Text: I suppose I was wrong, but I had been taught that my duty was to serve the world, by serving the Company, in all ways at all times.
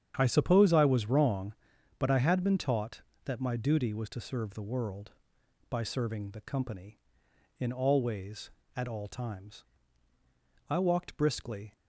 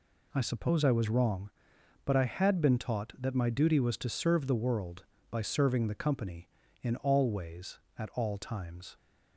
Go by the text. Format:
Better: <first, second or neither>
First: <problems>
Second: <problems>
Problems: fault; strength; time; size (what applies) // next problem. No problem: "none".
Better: second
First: starts louder than the rest; strong; until 1.1 s; 8.5 dB // goes on to say "I walked briskly"; noticeable; from 10.6 s on; 1.0 s long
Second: none